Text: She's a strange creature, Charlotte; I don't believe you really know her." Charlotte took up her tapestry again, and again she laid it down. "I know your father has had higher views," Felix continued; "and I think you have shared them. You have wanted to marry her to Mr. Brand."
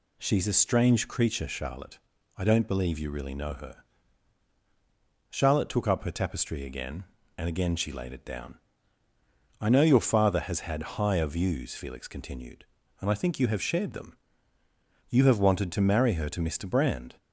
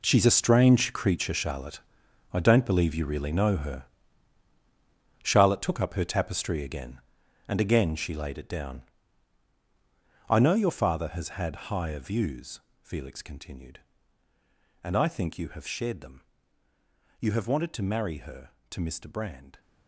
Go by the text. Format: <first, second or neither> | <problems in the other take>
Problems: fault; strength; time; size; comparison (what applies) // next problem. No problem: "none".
first | gets quieter; strong; throughout; 13.5 dB